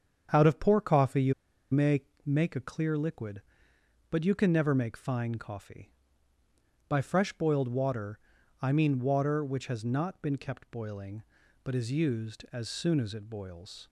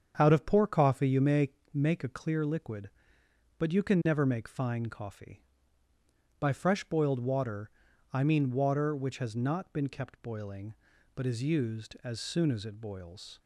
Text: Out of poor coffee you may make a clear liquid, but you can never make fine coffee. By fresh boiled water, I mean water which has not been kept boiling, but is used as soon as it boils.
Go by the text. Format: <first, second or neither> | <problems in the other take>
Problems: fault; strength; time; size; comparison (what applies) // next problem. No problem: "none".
second | starts louder than the rest; strong; until 1.3 s; 7.5 dB; strong in the second // pauses between "you" and "may"; at 1.3 s; 0.38 s long // pauses between "may" and "make"; slight; at 2.0 s; 0.24 s long; slight in the second